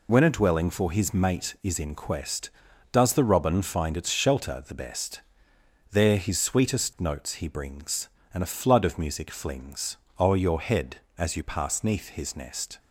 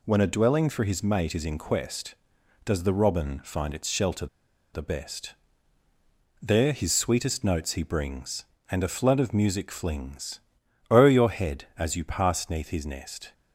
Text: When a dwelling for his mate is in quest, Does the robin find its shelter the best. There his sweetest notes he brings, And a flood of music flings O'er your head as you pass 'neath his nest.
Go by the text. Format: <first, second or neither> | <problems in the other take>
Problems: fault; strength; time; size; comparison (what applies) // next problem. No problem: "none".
first | pauses between "shelter" and "the"; noticeable; at 4.2 s; 0.47 s long // pauses between "flings" and "O'er"; noticeable; at 10.3 s; 0.50 s long; slight in the first